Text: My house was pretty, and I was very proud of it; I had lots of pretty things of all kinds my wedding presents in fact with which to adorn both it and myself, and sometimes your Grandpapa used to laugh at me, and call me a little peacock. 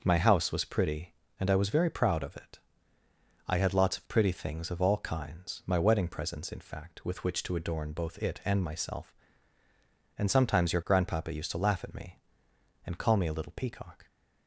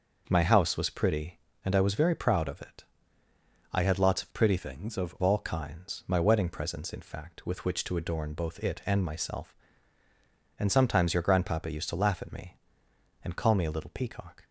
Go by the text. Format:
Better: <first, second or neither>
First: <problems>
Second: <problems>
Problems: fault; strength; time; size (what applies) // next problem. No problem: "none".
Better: first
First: none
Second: changes voice from "things" to "of"; from 4.5 to 5.1 s; 0.6 s long